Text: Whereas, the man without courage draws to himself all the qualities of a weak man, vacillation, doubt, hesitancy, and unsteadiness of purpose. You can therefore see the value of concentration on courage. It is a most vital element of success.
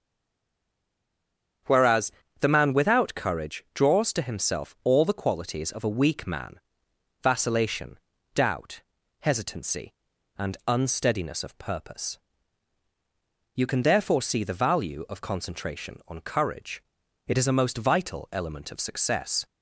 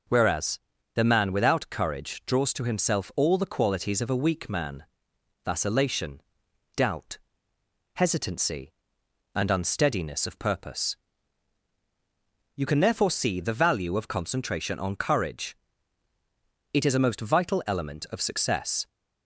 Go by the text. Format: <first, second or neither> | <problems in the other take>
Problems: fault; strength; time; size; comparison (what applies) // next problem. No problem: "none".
second | stays silent before the first word; noticeable; until 1.6 s; 1.6 s long // starts louder than the rest; strong; until 2.9 s; 8 dB